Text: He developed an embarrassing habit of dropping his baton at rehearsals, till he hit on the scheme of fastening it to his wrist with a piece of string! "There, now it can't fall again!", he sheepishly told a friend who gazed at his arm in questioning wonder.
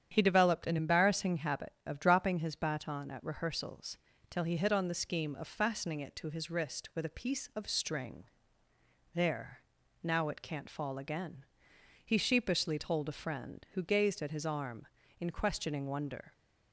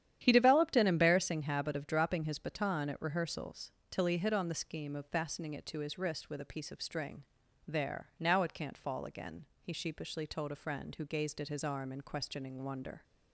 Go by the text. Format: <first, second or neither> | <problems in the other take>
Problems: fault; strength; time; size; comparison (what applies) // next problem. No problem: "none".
neither | starts louder than the rest; strong; the same in both